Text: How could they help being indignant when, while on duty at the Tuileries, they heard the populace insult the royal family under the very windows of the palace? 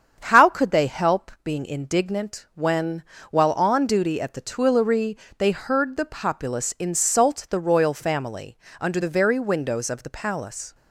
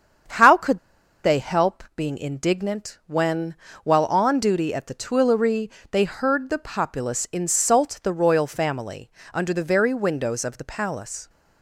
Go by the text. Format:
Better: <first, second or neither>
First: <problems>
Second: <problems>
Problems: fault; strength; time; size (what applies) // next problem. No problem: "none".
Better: first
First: starts louder than the rest; strong; until 1.2 s; 7.5 dB // pauses between "family" and "under"; slight; at 8.5 s; 0.22 s long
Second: starts louder than the rest; strong; until 1.7 s; 7.5 dB // pauses between "could" and "they"; at 0.7 s; 0.44 s long // pauses between "family" and "under"; slight; at 9.1 s; 0.22 s long